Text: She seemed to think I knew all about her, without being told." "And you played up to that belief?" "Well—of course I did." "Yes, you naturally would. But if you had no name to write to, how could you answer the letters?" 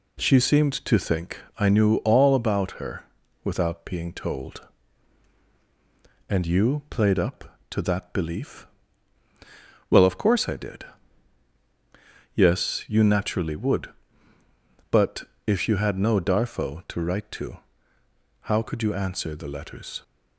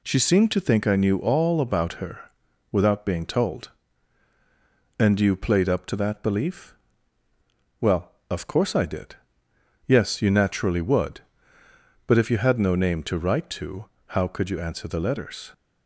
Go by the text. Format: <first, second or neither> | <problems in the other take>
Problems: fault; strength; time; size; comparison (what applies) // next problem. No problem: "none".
second | pauses between "think" and "I"; slight; at 1.3 s; 0.20 s long // pauses between "But" and "if"; slight; at 15.2 s; 0.24 s long // says "darfo" for "name"; at 16.1 s